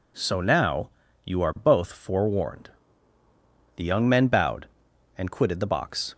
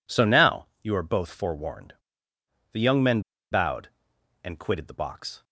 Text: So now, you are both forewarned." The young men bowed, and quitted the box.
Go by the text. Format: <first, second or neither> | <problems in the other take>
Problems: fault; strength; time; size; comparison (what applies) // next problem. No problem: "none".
first | pauses between "men" and "bowed"; slight; at 3.2 s; 0.30 s long